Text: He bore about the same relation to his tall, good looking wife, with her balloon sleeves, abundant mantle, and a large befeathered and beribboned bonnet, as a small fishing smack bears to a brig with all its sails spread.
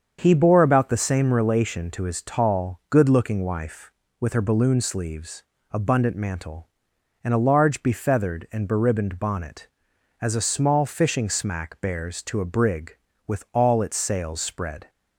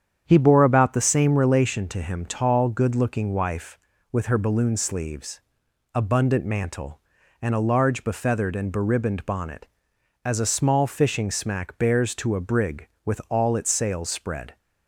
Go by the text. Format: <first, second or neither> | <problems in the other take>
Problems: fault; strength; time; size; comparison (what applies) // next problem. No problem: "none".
first | starts louder than the rest; strong; until 1.2 s; 8.5 dB; also in the first // says "him" for "his"; at 2.0 s